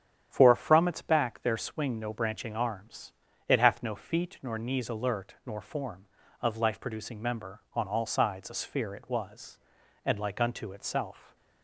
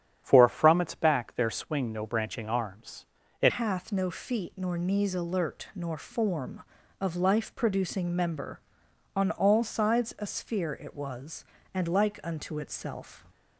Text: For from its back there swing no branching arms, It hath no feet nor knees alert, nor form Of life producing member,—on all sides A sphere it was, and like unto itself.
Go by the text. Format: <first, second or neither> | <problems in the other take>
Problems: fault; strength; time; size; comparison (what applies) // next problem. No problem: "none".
first | starts louder than the rest; strong; until 1.2 s; 9.5 dB; strong in the first // changes voice at "hath"; from 3.4 s on; 9.8 s long